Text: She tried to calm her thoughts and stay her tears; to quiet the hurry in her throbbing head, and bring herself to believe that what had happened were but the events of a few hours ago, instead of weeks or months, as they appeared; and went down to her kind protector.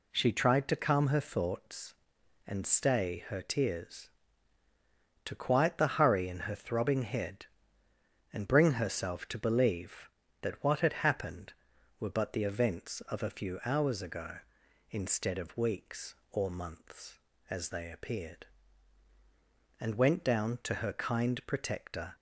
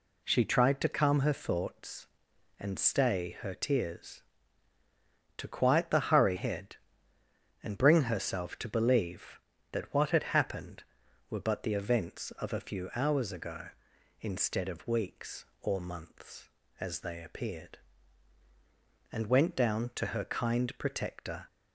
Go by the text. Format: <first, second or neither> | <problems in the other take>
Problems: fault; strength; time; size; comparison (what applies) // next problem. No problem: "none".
first | skips "in her throbbing"; at 6.3 s